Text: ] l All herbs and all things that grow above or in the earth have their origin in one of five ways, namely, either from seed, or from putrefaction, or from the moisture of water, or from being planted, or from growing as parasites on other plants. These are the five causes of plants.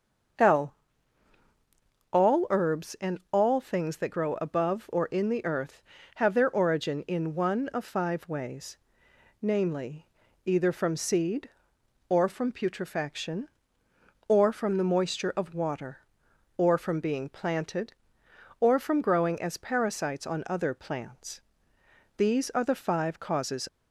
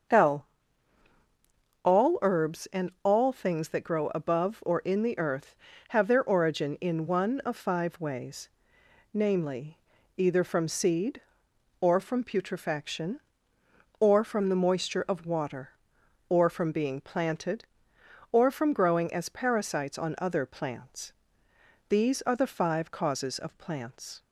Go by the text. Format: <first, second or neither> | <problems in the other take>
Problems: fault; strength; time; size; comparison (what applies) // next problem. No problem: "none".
second | starts louder than the rest; until 2.7 s; 7 dB; also in the second // pauses between "l" and "All"; strong; at 0.7 s; 1.3 s long; strong in the second // stops before "of plants"; at 23.6 s